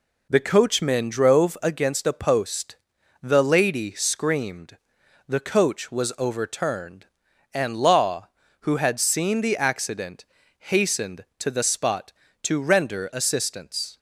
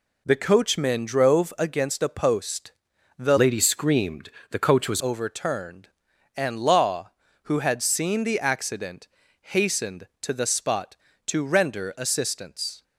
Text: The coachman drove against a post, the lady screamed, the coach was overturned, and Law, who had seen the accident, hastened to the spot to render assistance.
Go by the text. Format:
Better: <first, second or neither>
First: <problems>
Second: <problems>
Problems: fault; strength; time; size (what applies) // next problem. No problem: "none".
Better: first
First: none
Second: changes voice from "lady" to "was"; from 3.3 to 5.0 s; 1.7 s long